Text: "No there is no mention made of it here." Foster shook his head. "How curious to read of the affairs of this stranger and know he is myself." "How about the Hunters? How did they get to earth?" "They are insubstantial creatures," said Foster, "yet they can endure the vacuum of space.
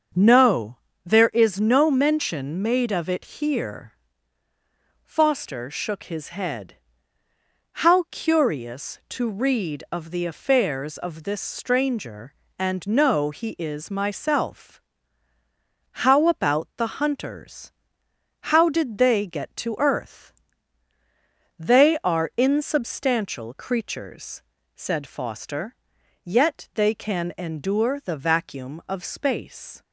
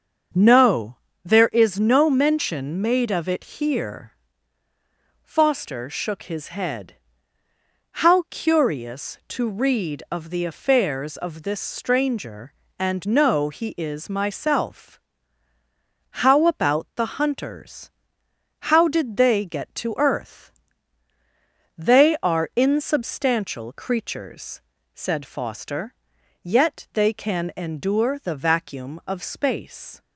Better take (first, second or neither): neither